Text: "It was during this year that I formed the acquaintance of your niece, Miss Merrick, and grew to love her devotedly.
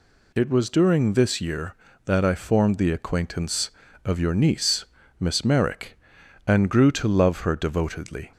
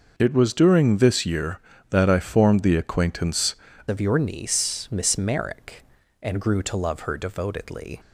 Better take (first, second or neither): first